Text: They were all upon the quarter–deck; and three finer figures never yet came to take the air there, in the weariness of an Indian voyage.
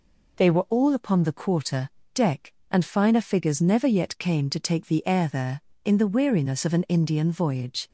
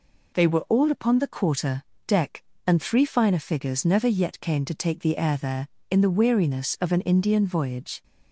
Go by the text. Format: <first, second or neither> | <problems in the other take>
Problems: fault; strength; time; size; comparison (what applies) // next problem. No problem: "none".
second | skips "three"; at 2.8 s